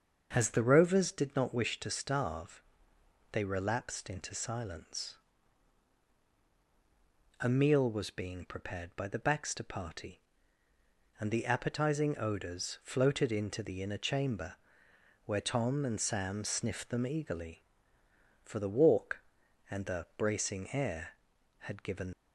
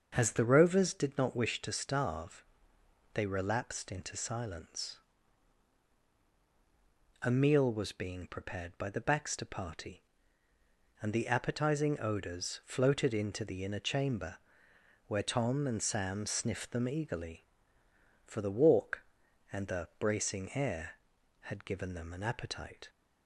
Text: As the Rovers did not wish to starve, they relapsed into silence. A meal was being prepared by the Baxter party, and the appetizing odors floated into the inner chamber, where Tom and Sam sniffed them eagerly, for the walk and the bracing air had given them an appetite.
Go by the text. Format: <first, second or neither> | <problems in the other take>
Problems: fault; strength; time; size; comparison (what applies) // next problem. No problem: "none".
second | starts louder than the rest; until 1.3 s; 6.5 dB; also in the second // stops before "them an appetite"; at 22.1 s